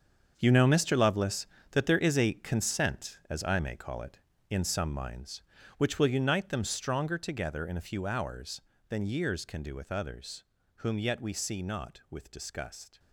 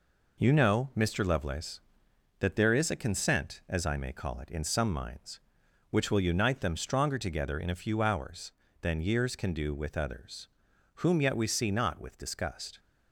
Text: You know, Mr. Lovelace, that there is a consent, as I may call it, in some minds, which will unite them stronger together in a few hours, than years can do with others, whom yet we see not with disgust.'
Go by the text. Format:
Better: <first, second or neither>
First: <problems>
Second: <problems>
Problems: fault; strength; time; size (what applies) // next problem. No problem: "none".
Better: second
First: gets quieter; strong; throughout; 12.5 dB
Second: none